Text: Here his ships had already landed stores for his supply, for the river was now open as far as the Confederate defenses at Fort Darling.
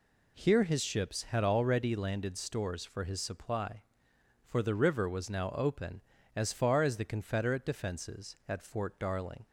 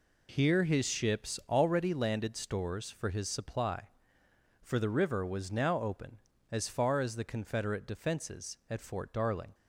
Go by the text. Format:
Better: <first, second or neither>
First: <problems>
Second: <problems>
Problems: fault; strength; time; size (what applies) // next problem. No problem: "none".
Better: first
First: none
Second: skips "had"; at 1.4 s